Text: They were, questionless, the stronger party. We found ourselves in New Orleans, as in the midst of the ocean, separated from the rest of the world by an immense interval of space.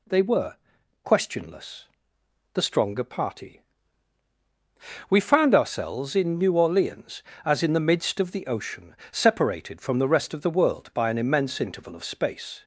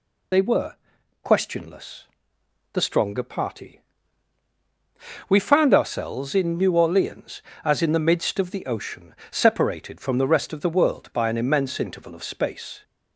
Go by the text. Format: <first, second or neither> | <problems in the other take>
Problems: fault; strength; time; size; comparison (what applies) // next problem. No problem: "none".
first | loses the start of "They"; at 0.3 s; 70 ms